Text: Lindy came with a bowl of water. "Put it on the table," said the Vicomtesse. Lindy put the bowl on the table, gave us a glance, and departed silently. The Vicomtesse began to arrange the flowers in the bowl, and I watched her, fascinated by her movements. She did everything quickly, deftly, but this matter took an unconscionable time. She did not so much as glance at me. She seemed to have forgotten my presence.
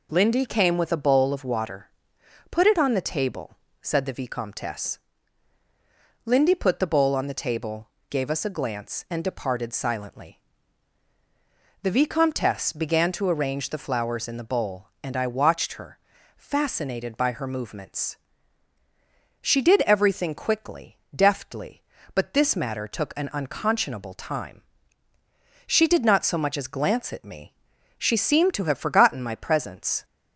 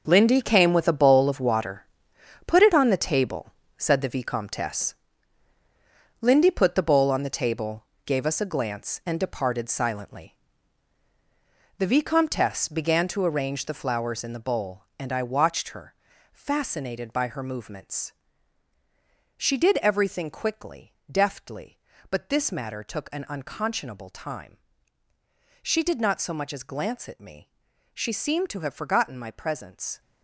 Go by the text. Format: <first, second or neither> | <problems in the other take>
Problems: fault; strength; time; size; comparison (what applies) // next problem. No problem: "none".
first | gets quieter; strong; throughout; 11.5 dB